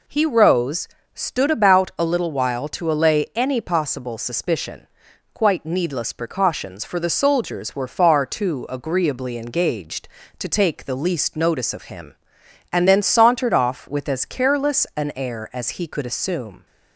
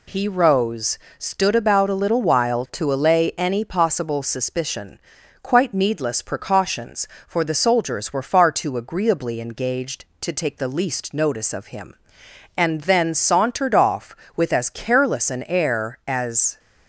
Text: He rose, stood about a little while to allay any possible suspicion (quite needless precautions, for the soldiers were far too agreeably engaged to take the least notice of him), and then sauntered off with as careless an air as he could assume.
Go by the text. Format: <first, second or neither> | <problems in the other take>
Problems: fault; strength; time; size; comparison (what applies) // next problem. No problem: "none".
first | stops before "he could assume"; at 16.5 s